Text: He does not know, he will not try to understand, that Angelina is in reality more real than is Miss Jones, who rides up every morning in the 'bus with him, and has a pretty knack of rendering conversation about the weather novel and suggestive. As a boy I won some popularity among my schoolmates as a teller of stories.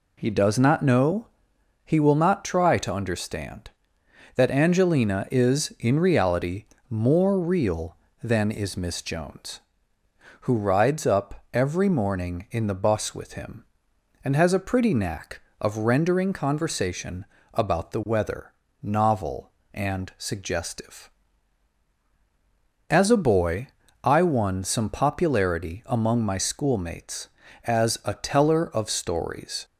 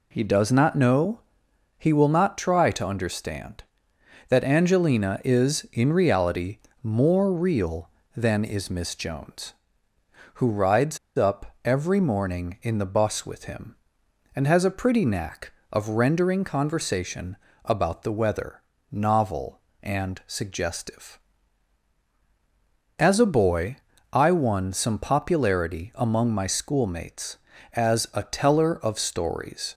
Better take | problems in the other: first | pauses between "reality" and "more"; slight; at 6.5 s; 0.24 s long; slight in the first // pauses between "rides" and "up"; slight; at 10.9 s; 0.19 s long // pauses between "conversation" and "about"; slight; at 17.3 s; 0.28 s long; slight in the first // pauses between "weather" and "novel"; slight; at 18.6 s; 0.30 s long; slight in the first // pauses between "boy" and "I"; slight; at 23.7 s; 0.34 s long; slight in the first

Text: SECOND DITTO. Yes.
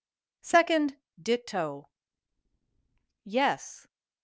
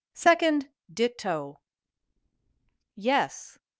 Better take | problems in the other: neither | pauses between "SECOND" and "DITTO"; slight; the same in both

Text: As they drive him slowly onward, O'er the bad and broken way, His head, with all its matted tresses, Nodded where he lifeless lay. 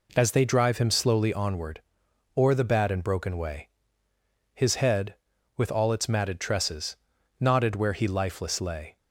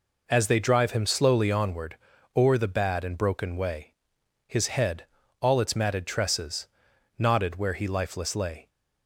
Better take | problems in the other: first | skips "with"; at 5.2 s

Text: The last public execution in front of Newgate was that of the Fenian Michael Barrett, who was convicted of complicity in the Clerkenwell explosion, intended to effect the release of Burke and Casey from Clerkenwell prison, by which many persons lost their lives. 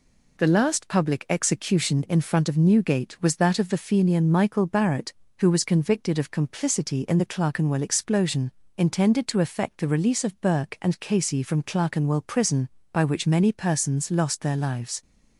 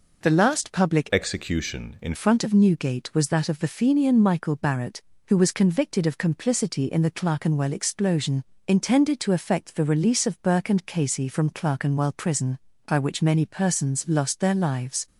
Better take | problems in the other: first | changes voice from "execution" to "in"; from 1.1 to 2.1 s; 1.0 s long

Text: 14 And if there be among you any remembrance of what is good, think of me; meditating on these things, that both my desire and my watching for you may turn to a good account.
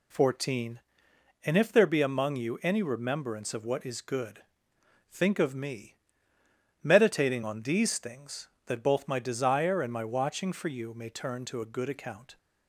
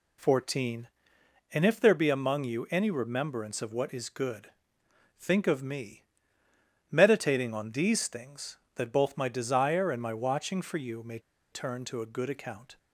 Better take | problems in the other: first | pauses between "may" and "turn"; slight; at 11.1 s; 0.32 s long

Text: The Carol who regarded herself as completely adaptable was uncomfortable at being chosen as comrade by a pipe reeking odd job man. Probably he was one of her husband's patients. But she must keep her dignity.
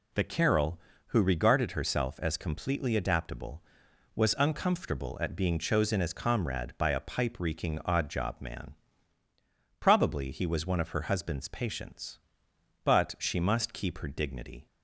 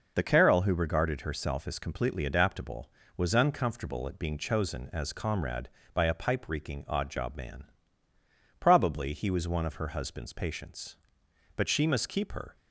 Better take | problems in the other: first | stops before "dignity"; at 12.5 s

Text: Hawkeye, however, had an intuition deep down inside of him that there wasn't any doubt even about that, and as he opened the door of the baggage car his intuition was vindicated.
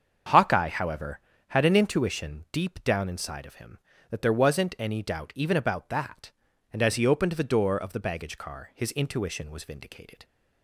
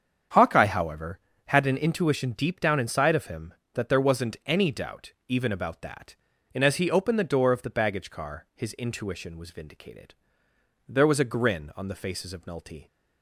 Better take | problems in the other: first | starts louder than the rest; strong; until 1.5 s; 8 dB; strong in the first // pauses between "doubt" and "even"; slight; at 5.1 s; 0.16 s long // goes on to say "There was a grin on the faces of Nulty"; strong; from 10.8 s on; 2.0 s long

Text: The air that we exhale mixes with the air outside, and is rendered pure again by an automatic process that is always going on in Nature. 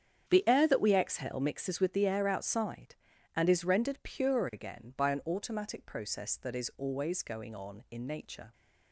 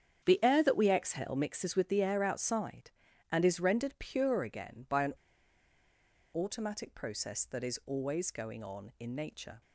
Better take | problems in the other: first | starts louder than the rest; strong; until 1.2 s; 8.5 dB; strong in the first // pauses between "an" and "automatic"; at 5.1 s; 1.2 s long

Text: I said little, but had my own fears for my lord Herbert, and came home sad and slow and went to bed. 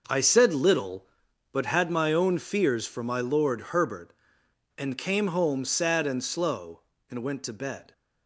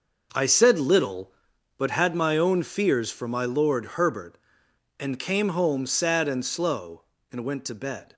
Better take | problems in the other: neither | none

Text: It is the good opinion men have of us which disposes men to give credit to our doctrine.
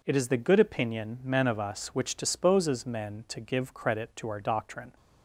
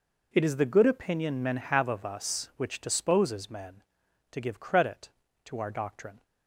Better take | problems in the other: second | skips "have"; at 1.4 s

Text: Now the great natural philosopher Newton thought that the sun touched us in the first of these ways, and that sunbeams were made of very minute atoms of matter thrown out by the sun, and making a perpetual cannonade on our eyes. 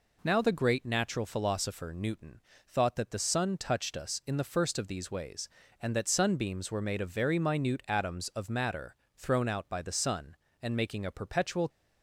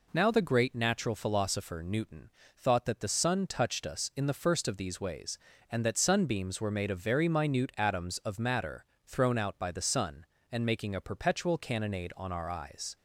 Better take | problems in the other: second | pauses between "Newton" and "thought"; slight; at 2.4 s; 0.26 s long; slight in the second // pauses between "matter" and "thrown"; slight; at 8.9 s; 0.20 s long; slight in the second // stops before "cannonade on our eyes"; at 11.6 s

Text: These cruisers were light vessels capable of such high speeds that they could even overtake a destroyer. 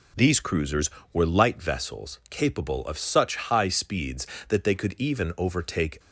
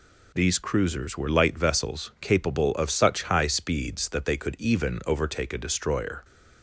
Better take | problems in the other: second | stops before "a destroyer"; at 5.9 s

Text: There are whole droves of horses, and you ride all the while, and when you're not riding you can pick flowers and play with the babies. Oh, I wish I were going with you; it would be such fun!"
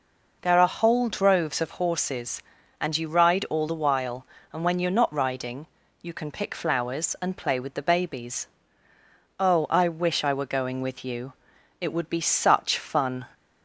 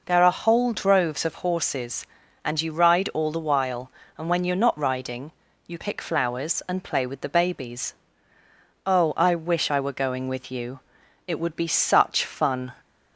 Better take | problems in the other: first | pauses between "riding" and "you"; slight; at 5.3 s; 0.34 s long; slight in the first // skips "can"; at 5.7 s

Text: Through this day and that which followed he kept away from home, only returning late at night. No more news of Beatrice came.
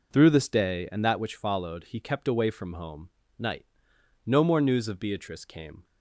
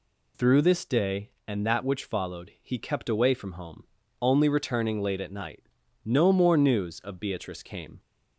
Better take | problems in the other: second | skips "only returning late at"; at 3.2 s

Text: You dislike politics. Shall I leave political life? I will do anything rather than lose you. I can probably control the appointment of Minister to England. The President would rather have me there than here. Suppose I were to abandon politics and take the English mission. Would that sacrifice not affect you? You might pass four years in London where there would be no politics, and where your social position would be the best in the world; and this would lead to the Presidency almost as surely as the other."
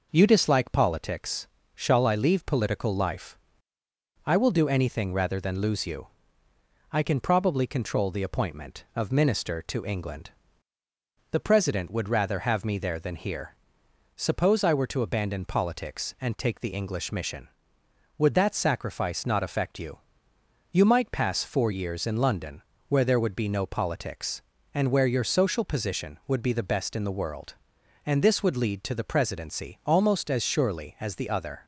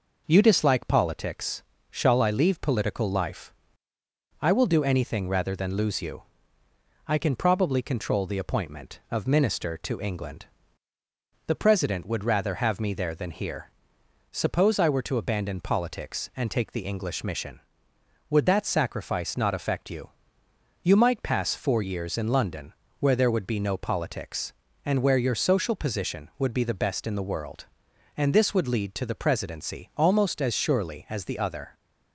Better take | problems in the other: neither | pauses between "London" and "where"; slight; the same in both

